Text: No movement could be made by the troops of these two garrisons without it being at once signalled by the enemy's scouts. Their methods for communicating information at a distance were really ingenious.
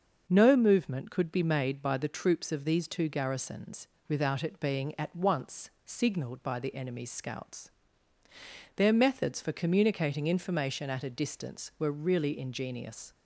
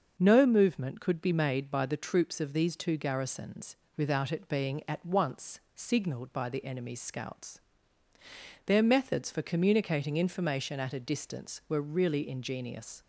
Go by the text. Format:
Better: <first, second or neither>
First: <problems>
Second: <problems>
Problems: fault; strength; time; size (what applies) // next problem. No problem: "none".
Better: neither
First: starts louder than the rest; until 1.3 s; 6.5 dB // pauses between "garrisons" and "without"; slight; at 3.8 s; 0.20 s long // pauses between "once" and "signalled"; slight; at 5.6 s; 0.16 s long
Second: starts louder than the rest; until 1.2 s; 6.5 dB // pauses between "garrisons" and "without"; slight; at 3.7 s; 0.20 s long // pauses between "once" and "signalled"; slight; at 5.5 s; 0.16 s long